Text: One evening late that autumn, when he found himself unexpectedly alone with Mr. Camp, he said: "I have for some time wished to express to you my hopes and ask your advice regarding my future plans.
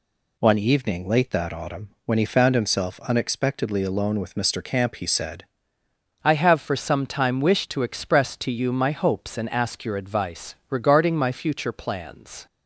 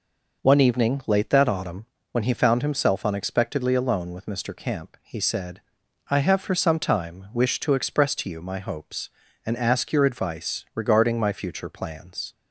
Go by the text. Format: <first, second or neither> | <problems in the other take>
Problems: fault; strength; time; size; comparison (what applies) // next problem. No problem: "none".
second | changes voice at "I"; from 6.2 s on; 6.2 s long // pauses between "advice" and "regarding"; slight; at 10.5 s; 0.16 s long